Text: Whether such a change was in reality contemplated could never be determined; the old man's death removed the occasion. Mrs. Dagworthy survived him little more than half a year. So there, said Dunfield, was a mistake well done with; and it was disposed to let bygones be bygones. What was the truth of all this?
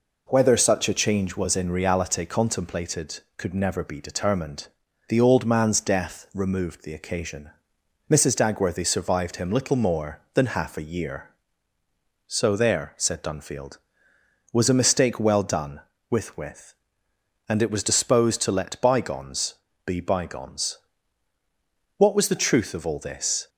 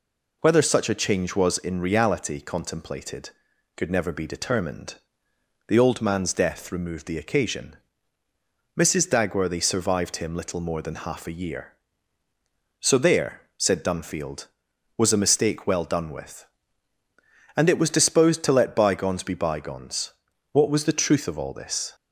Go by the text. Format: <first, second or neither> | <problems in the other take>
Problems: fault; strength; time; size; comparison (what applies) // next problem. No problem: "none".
second | says "with" twice; at 16.3 s // pauses between "bygones" and "be"; slight; at 19.5 s; 0.30 s long